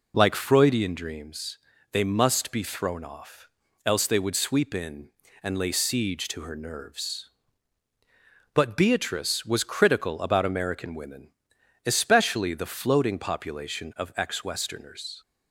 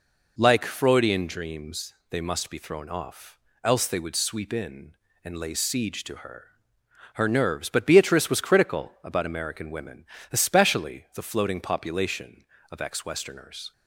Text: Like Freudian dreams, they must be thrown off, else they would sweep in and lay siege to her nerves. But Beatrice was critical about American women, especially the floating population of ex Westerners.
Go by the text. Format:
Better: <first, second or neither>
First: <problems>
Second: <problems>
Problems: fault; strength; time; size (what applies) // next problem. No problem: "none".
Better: first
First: none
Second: says "her" twice; at 7.1 s